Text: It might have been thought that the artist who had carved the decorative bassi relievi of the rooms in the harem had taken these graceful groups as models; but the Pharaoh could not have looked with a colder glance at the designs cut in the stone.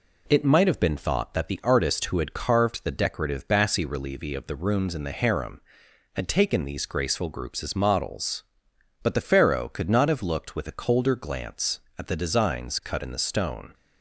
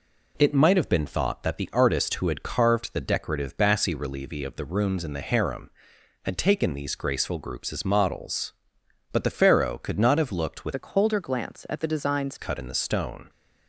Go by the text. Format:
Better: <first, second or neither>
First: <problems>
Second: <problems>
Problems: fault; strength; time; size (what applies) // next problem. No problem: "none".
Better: first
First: none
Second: changes voice from "a" to "designs"; from 10.7 to 12.3 s; 1.6 s long